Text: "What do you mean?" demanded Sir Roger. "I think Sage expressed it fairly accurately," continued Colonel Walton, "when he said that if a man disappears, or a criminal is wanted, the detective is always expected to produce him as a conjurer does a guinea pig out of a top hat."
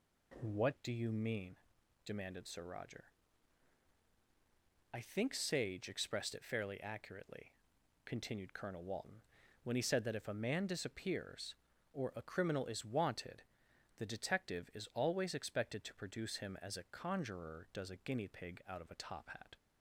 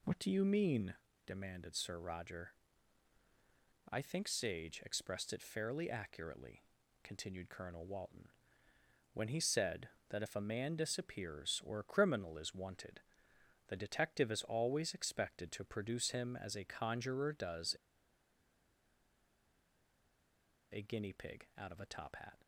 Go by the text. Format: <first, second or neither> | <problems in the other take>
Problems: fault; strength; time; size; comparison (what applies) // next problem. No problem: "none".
first | pauses between "does" and "a"; strong; at 17.7 s; 2.9 s long